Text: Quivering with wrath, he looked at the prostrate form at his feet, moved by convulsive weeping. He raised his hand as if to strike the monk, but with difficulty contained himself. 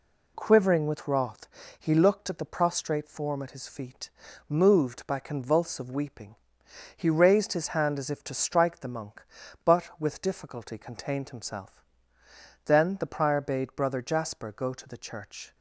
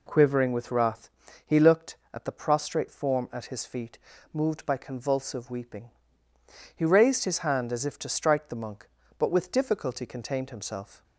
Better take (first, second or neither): second